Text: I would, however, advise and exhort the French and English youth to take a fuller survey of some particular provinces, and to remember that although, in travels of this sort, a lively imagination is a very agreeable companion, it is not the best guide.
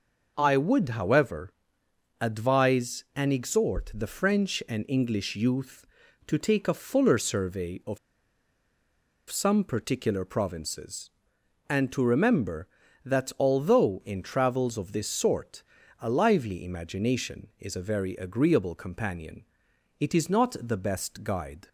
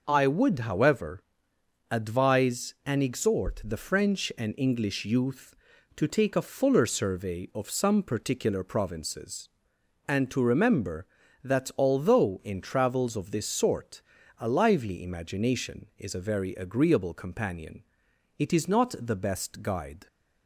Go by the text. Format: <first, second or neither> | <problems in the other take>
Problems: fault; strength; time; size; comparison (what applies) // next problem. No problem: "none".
second | pauses between "of" and "some"; strong; at 7.9 s; 1.3 s long